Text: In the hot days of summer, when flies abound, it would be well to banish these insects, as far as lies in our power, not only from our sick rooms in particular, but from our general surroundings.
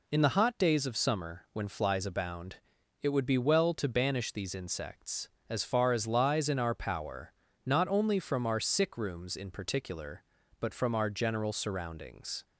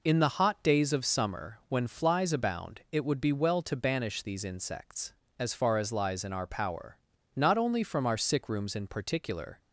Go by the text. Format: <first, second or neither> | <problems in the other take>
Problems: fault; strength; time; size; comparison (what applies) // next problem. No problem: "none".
first | stops before "but from our general surroundings"; at 9.5 s